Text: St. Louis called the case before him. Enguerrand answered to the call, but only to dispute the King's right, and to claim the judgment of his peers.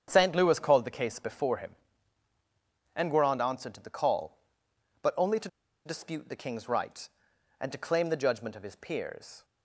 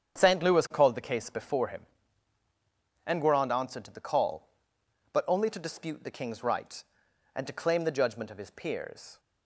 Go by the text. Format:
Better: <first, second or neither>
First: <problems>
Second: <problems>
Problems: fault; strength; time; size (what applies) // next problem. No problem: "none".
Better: second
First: starts louder than the rest; strong; until 1.0 s; 8 dB // pauses between "to" and "dispute"; at 5.4 s; 0.38 s long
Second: starts louder than the rest; strong; until 1.2 s; 8 dB